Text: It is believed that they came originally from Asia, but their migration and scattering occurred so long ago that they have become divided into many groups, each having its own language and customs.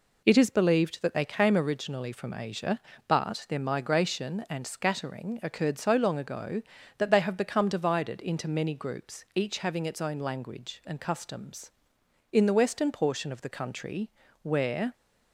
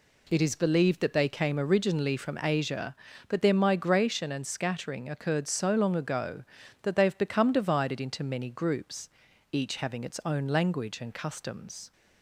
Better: second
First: goes on to say "In the western portion of the country where"; strong; from 12.3 s on; 2.6 s long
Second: none

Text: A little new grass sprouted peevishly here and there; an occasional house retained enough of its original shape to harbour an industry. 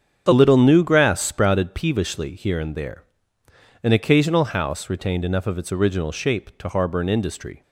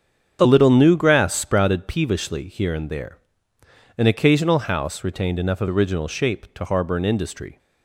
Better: first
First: starts louder than the rest; strong; until 1.3 s; 7.5 dB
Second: starts louder than the rest; strong; until 1.4 s; 7.5 dB // skips "its"; at 5.6 s

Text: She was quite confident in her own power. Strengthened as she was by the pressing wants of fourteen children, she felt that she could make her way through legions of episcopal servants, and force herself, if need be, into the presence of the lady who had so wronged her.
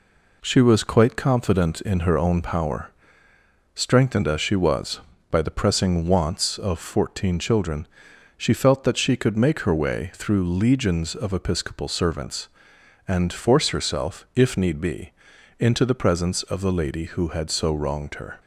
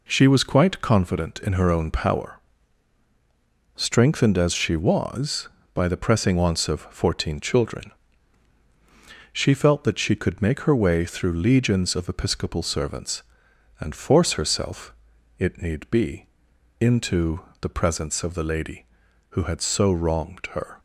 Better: first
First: none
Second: says "it" for "if"; at 15.3 s // pauses between "into" and "the"; slight; at 17.3 s; 0.20 s long

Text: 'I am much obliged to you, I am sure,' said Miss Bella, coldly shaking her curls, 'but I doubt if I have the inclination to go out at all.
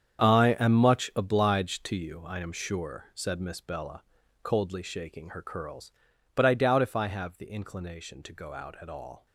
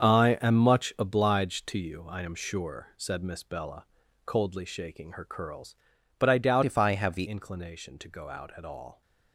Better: first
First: starts louder than the rest; strong; until 1.2 s; 8 dB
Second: starts louder than the rest; strong; until 1.0 s; 7 dB // changes voice from "if" to "the"; from 6.6 to 7.2 s; 0.6 s long

